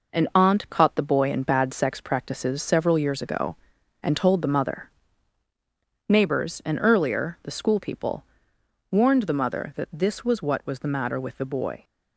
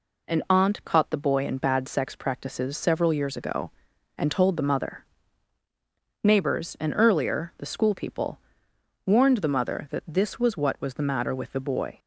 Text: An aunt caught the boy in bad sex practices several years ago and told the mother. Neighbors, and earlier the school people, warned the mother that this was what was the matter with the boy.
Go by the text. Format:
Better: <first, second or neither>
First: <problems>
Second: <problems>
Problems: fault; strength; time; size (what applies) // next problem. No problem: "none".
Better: second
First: gets quieter; noticeable; throughout; 5 dB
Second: none